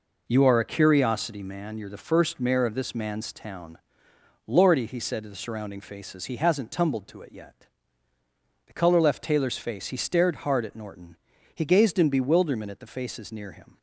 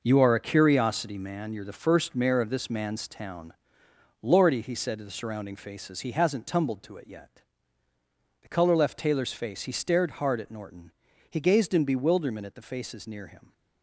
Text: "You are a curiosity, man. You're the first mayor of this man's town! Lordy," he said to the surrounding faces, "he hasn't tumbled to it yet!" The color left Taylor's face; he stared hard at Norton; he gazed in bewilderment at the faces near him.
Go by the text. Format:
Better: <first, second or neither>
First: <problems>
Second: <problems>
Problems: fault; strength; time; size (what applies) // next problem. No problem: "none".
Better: first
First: none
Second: gets quieter; strong; throughout; 9 dB